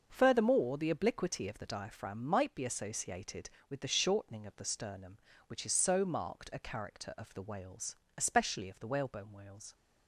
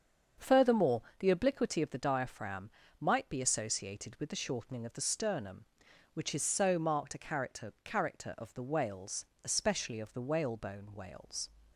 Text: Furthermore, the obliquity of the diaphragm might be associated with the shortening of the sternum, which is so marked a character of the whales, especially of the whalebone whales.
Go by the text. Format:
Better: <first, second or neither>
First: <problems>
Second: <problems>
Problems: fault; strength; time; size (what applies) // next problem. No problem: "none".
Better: first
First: starts louder than the rest; until 1.1 s; 6.5 dB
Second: starts louder than the rest; strong; until 1.5 s; 7 dB // pauses between "diaphragm" and "might"; slight; at 2.7 s; 0.30 s long // says "character" twice; at 7.8 s